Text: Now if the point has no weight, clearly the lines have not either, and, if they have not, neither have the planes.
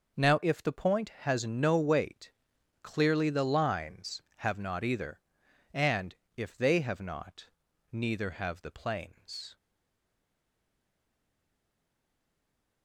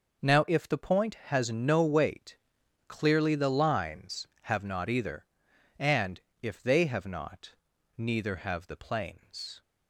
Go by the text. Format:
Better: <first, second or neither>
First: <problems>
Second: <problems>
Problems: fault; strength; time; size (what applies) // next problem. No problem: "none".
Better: second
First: starts louder than the rest; noticeable; until 1.3 s; 6 dB // stays silent after the last word; strong; from 9.5 s on; 3.3 s long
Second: starts louder than the rest; noticeable; until 1.4 s; 6 dB